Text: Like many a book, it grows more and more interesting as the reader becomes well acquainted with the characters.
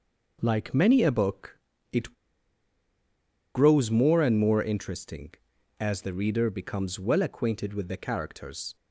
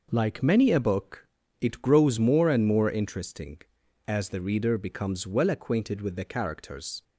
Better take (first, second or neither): second